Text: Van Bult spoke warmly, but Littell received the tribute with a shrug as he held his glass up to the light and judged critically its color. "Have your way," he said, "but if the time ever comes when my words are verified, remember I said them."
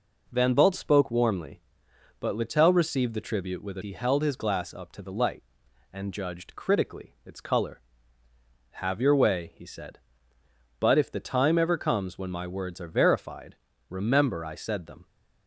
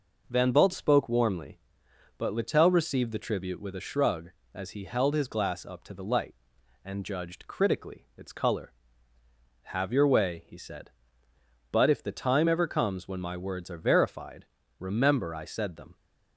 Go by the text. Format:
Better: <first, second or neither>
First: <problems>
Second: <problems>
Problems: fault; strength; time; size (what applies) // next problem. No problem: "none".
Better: second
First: skips "shrug as"; at 3.8 s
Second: none